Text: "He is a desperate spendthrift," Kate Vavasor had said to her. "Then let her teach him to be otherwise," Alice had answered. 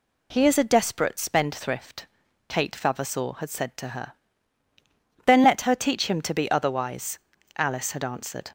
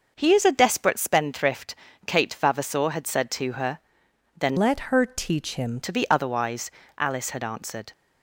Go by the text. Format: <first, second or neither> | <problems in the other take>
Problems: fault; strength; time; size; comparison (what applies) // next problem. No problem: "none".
first | changes voice from "let" to "him"; from 4.5 to 5.8 s; 1.3 s long